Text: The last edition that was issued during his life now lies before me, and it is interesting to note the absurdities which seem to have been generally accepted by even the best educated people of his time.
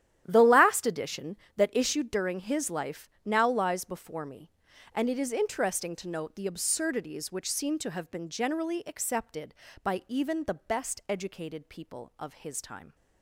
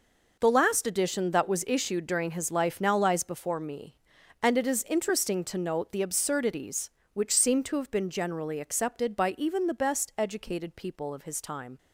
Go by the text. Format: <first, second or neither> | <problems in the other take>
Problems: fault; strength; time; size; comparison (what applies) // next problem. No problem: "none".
second | starts louder than the rest; strong; until 1.2 s; 11.5 dB // skips "was"; at 1.6 s // pauses between "life" and "now"; slight; at 3.0 s; 0.18 s long